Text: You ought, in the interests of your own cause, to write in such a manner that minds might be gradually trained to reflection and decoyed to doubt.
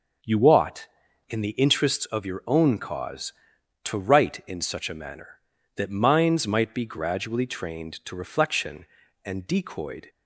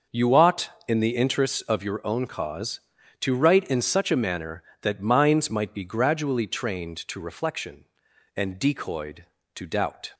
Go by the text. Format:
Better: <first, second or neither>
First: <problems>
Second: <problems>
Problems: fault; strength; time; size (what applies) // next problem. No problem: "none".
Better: second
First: stops before "to doubt"; at 10.0 s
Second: none